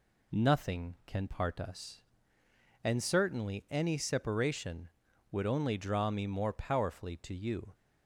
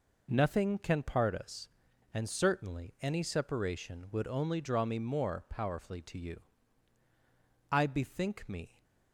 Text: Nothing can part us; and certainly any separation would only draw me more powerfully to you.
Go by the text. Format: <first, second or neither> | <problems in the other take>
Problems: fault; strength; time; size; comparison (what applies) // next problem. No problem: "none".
first | goes on to say "I bethink me"; noticeable; from 7.7 s on; 1.1 s long